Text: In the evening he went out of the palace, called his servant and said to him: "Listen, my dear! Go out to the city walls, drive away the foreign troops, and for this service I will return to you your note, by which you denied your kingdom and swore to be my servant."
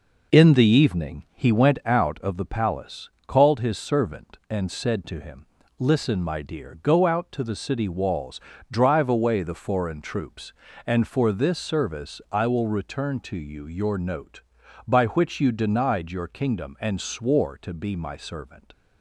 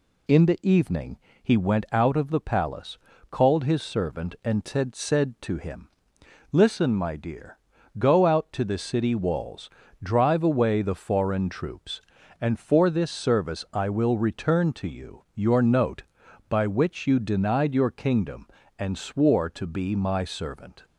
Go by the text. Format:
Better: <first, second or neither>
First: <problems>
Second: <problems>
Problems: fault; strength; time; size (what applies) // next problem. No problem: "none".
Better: first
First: none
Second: pauses between "evening" and "he"; slight; at 1.1 s; 0.22 s long // says "said" twice; at 4.9 s